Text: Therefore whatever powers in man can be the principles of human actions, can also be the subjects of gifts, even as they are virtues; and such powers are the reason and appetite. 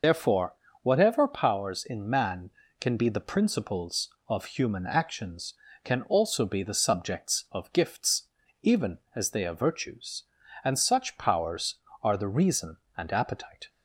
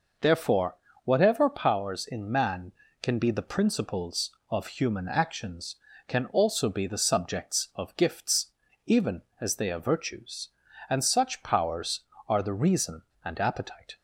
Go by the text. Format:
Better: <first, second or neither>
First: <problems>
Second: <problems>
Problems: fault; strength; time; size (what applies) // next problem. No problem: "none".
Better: second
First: loses the start of "Therefore"; at 0.0 s; 50 ms // pauses between "Therefore" and "whatever"; slight; at 0.5 s; 0.30 s long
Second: pauses between "Therefore" and "whatever"; slight; at 0.7 s; 0.30 s long